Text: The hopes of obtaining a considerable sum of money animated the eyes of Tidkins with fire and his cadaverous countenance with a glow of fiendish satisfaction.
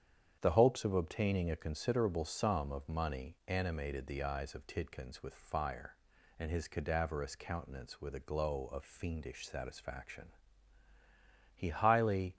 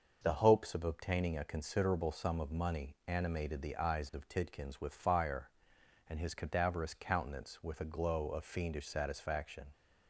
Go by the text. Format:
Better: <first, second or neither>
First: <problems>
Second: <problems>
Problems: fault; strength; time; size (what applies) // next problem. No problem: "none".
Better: second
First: starts louder than the rest; strong; until 1.4 s; 8.5 dB // goes on to say "He highly"; noticeable; from 11.5 s on; 0.82 s long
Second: starts louder than the rest; noticeable; until 1.2 s; 6 dB